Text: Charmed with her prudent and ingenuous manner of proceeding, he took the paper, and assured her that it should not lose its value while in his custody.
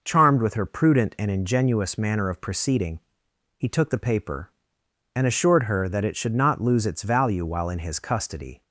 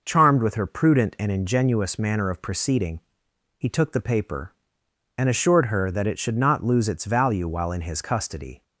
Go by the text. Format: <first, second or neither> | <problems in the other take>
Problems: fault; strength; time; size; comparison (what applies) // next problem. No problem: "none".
neither | none